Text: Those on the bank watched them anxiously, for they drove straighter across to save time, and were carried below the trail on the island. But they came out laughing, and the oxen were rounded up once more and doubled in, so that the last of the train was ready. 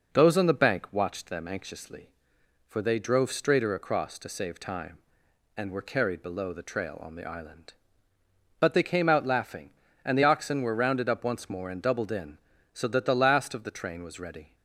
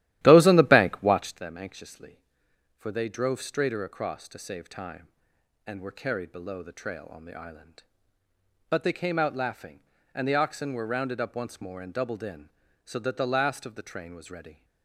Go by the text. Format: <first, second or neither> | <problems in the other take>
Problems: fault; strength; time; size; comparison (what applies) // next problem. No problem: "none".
first | starts louder than the rest; strong; until 1.4 s; 14 dB